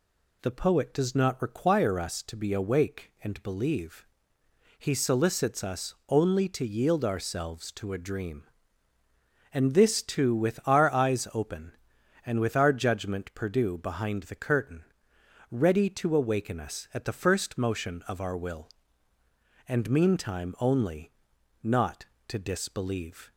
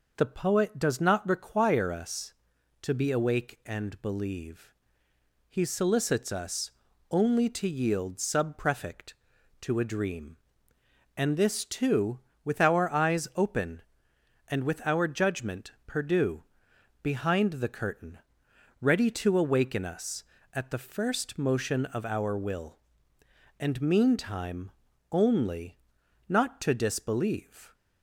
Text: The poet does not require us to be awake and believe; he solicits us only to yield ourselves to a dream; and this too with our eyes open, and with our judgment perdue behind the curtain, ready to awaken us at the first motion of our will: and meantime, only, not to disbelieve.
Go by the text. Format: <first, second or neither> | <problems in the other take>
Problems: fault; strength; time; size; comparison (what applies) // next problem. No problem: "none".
first | pauses between "us" and "only"; at 6.7 s; 0.40 s long // says "subprefect" for "ourselves"; at 8.1 s // pauses between "perdue" and "behind"; noticeable; at 16.4 s; 0.60 s long